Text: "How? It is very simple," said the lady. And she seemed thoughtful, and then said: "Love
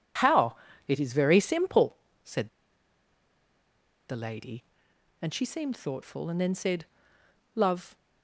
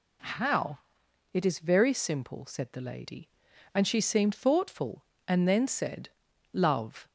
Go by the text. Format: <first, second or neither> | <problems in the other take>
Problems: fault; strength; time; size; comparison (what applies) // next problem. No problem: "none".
second | pauses between "said" and "the"; strong; at 2.4 s; 1.6 s long